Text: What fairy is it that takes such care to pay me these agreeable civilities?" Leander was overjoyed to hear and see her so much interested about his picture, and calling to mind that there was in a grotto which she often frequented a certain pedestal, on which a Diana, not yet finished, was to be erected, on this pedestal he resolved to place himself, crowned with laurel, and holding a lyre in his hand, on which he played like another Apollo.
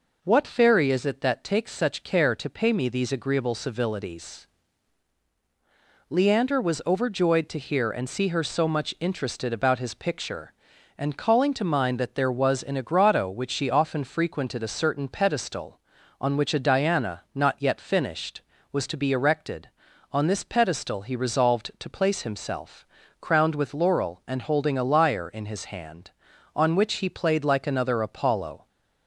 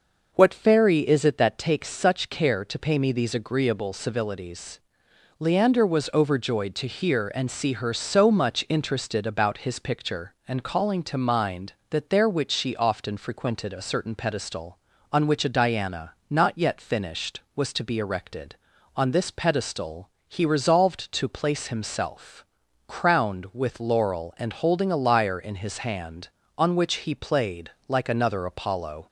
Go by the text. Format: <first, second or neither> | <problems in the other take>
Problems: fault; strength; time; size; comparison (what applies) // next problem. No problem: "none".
first | skips "was in a grotto"; at 12.2 s // pauses between "pedestal" and "he"; slight; at 20.0 s; 0.20 s long // pauses between "played" and "like"; slight; at 27.6 s; 0.16 s long